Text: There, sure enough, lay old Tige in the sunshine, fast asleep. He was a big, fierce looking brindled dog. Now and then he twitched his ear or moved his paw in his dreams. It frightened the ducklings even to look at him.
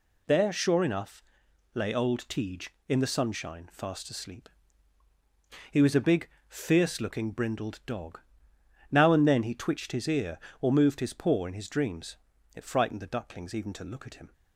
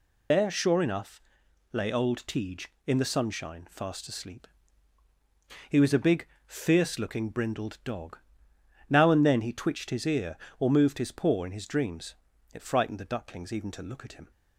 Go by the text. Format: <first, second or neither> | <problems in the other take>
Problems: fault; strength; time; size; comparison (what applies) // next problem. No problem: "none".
first | loses the start of "There"; at 0.3 s; 55 ms